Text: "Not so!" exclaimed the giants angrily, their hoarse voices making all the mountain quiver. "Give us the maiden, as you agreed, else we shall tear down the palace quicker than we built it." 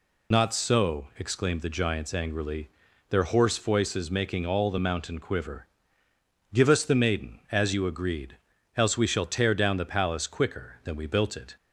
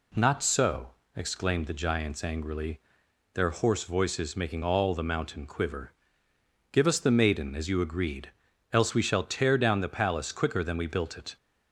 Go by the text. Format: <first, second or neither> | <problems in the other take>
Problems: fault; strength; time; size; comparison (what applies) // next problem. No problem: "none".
second | loses the start of "Not"; at 0.3 s; 60 ms